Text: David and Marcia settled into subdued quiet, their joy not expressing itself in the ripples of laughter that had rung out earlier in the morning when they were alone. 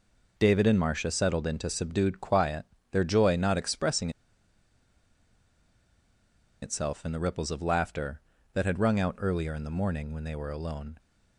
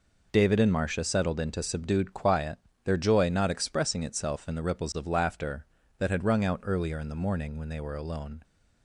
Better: second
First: pauses between "expressing" and "itself"; strong; at 4.1 s; 2.5 s long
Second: none

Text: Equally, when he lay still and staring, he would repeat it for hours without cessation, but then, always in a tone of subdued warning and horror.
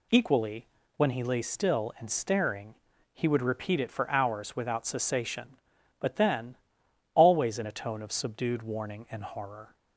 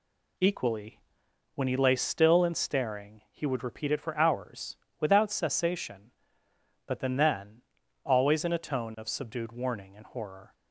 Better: first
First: none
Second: pauses between "hours" and "without"; slight; at 4.7 s; 0.22 s long // says "then" twice; at 7.1 s

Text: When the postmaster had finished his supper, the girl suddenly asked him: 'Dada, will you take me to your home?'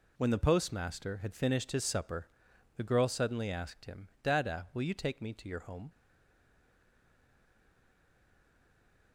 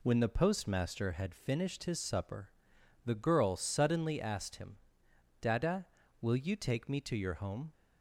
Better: second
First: stays silent after the last word; strong; from 5.8 s on; 3.3 s long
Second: none

